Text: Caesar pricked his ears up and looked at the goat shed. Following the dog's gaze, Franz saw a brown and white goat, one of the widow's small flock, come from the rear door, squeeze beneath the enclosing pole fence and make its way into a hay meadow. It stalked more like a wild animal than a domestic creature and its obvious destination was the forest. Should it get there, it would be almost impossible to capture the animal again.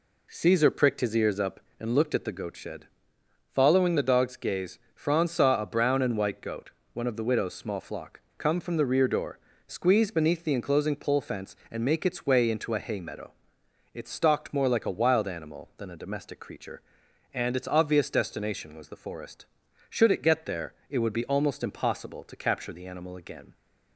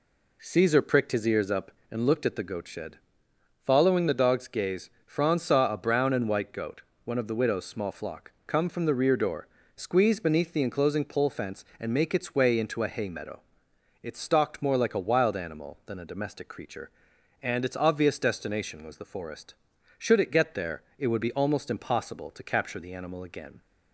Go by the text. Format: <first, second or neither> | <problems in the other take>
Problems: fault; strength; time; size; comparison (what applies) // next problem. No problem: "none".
neither | none